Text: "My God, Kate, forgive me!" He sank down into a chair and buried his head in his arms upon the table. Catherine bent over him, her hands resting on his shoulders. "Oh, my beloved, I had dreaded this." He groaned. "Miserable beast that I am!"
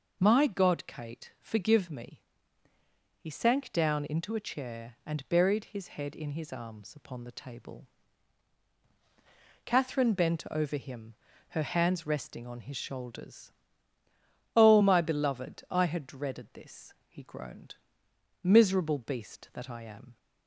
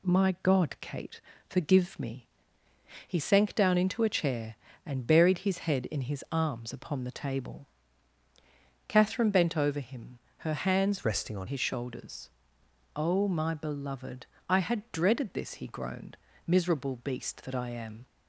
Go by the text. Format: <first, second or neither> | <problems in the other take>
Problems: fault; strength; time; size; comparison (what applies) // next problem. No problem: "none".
first | changes voice from "resting" to "on"; from 11.0 to 11.4 s; 0.4 s long